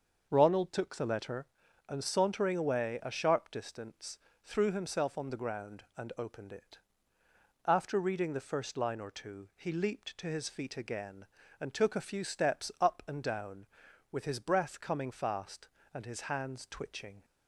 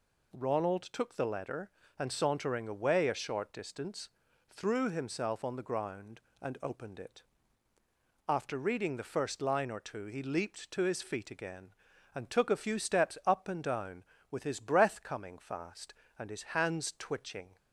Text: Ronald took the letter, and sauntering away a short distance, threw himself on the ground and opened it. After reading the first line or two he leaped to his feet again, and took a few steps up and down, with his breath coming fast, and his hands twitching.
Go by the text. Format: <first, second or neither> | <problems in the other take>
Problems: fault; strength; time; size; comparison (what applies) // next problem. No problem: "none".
second | starts louder than the rest; until 1.3 s; 6.5 dB // says "sharp" for "short"; at 3.1 s